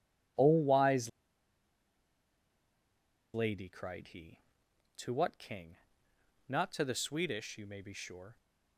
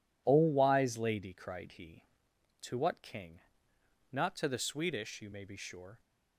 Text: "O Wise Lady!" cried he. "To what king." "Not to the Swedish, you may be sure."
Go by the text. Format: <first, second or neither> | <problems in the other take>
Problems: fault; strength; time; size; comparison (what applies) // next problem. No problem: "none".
second | pauses between "Wise" and "Lady"; strong; at 1.0 s; 2.2 s long